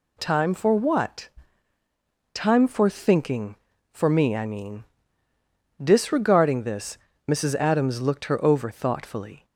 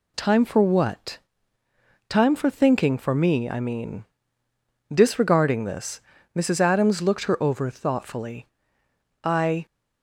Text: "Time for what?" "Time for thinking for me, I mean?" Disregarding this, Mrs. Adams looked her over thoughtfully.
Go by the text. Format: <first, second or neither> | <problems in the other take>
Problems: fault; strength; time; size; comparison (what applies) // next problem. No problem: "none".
first | goes on to say "I"; slight; from 9.2 s on; 0.40 s long